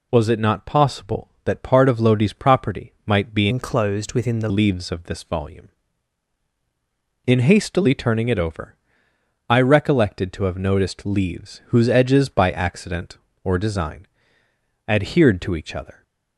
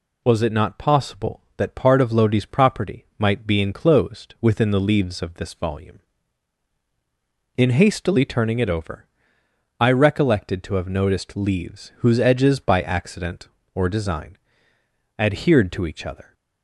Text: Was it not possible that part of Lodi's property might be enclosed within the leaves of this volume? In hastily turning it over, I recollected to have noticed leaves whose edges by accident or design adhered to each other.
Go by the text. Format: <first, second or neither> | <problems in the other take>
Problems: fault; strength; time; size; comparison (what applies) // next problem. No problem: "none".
second | changes voice from "enclosed" to "the"; from 3.4 to 4.4 s; 1.0 s long // pauses between "design" and "adhered"; noticeable; at 14.0 s; 0.82 s long; noticeable in the second